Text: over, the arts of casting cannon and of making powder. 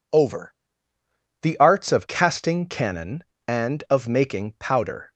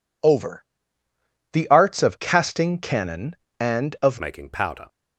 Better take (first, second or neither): first